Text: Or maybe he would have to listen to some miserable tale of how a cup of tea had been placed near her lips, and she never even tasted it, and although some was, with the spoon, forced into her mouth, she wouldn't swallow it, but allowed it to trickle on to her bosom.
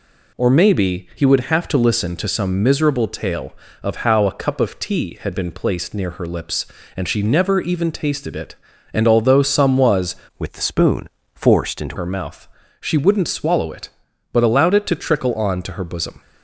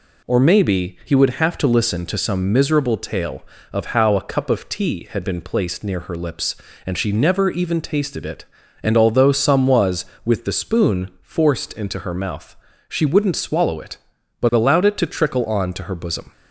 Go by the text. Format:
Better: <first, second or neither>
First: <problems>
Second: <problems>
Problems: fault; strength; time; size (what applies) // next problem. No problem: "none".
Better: second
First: changes voice from "with" to "into"; from 10.3 to 11.9 s; 1.6 s long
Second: none